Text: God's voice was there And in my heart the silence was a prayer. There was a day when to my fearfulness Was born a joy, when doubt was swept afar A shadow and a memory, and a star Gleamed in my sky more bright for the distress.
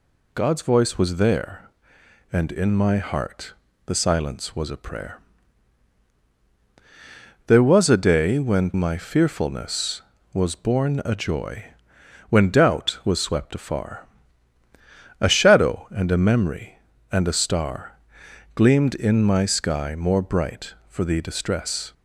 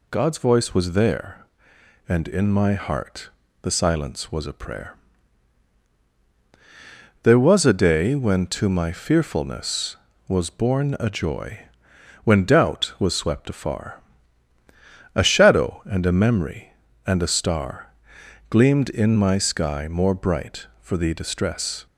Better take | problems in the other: second | pauses between "heart" and "the"; slight; at 3.5 s; 0.32 s long; slight in the second // skips "to"; at 8.7 s // pauses between "afar" and "A"; at 14.0 s; 1.1 s long; also in the second // pauses between "star" and "Gleamed"; noticeable; at 17.9 s; 0.58 s long; noticeable in the second

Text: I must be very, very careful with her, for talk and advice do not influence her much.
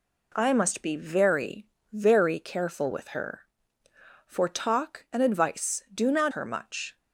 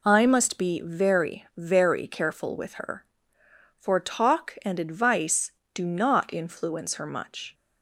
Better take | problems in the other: second | skips "influence"; at 6.3 s

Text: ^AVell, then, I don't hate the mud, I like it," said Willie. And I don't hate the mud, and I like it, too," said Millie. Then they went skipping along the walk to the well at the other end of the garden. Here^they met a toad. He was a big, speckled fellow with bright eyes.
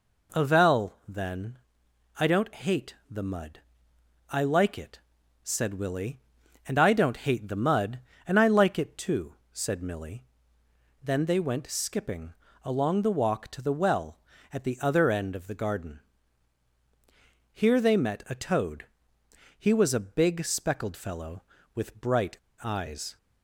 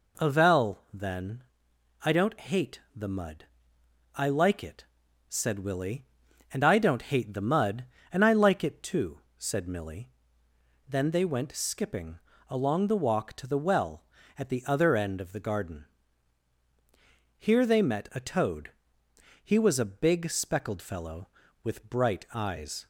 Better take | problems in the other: second | pauses between "skipping" and "along"; slight; at 12.3 s; 0.30 s long; slight in the second // pauses between "bright" and "eyes"; slight; at 22.3 s; 0.26 s long

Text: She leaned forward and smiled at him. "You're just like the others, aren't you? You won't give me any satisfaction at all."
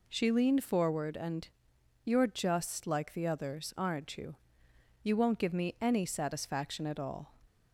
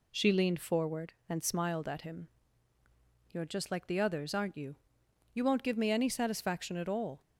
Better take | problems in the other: second | skips "smiled at him"; at 1.7 s

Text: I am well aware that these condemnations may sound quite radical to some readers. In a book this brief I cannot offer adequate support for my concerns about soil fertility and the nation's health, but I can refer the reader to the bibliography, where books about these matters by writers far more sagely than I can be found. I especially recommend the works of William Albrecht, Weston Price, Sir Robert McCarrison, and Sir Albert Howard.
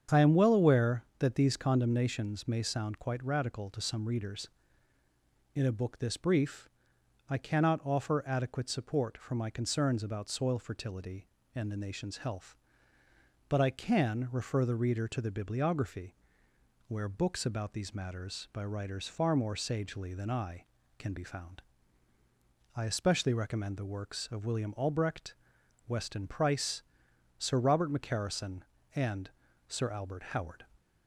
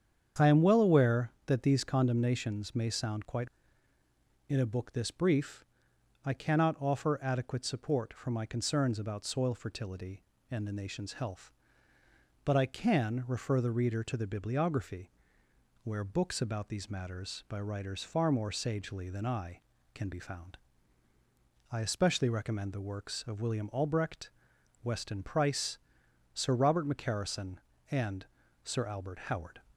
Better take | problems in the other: first | starts louder than the rest; strong; until 1.5 s; 8 dB; strong in the first // skips "radical to some readers"; at 3.9 s // pauses between "brief" and "I"; noticeable; at 5.6 s; 0.58 s long; noticeable in the first // pauses between "and" and "Sir"; at 28.2 s; 0.42 s long; also in the first

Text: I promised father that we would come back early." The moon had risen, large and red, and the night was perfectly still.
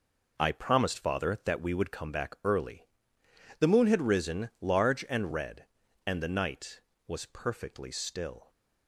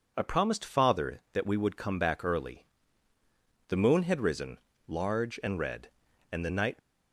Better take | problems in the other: first | stops before "was perfectly still"; at 6.7 s

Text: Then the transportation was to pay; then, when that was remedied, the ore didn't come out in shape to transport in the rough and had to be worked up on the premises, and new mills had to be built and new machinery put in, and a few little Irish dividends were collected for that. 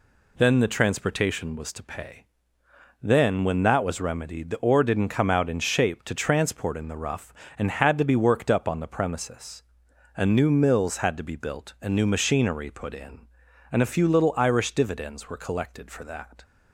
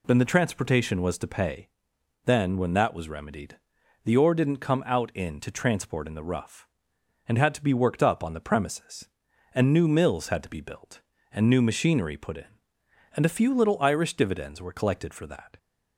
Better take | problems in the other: first | skips "shape"; at 5.3 s

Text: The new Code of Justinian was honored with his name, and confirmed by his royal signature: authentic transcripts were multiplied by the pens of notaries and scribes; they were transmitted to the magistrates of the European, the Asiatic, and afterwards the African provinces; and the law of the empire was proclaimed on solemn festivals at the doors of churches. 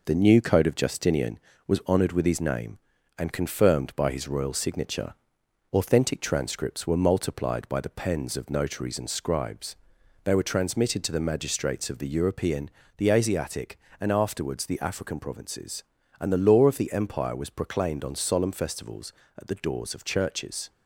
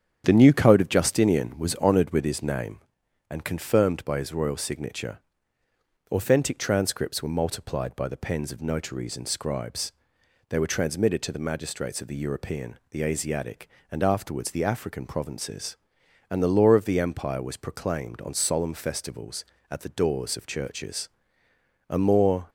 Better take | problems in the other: first | starts louder than the rest; strong; until 1.2 s; 8.5 dB // goes on to say "A more"; noticeable; from 21.8 s on; 0.62 s long

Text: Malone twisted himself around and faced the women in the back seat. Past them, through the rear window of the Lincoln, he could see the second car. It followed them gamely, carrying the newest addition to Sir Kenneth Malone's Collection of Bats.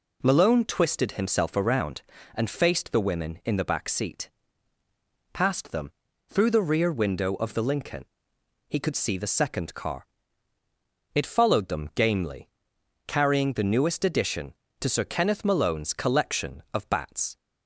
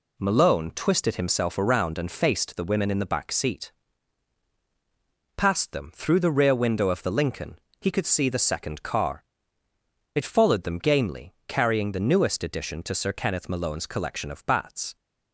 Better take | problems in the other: neither | none

